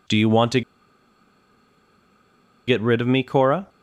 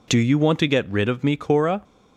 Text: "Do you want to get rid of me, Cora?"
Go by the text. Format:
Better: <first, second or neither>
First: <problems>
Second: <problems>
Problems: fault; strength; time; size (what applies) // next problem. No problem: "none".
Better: second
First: pauses between "to" and "get"; strong; at 0.6 s; 2.0 s long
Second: none